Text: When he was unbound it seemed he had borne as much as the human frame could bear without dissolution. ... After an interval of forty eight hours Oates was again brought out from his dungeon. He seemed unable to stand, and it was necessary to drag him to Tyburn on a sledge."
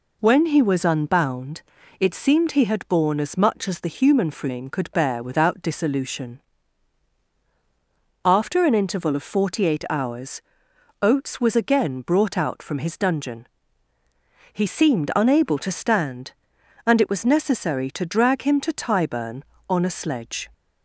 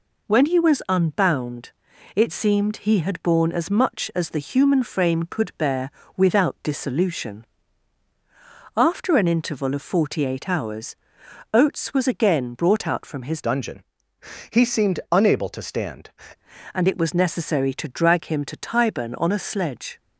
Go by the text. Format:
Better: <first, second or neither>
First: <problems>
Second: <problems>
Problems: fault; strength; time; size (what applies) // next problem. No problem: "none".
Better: first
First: pauses between "unbound" and "it"; slight; at 1.6 s; 0.36 s long // pauses between "hours" and "Oates"; noticeable; at 10.4 s; 0.60 s long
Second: pauses between "unbound" and "it"; at 1.7 s; 0.44 s long // pauses between "bear" and "without"; slight; at 5.8 s; 0.28 s long // pauses between "hours" and "Oates"; noticeable; at 10.9 s; 0.58 s long // changes voice from "dungeon" to "stand"; from 13.4 to 16.0 s; 2.6 s long